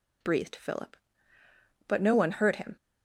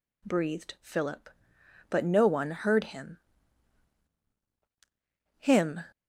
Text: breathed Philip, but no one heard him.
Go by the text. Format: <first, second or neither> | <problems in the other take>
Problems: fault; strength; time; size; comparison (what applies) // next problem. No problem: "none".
first | says "him" twice; at 5.3 s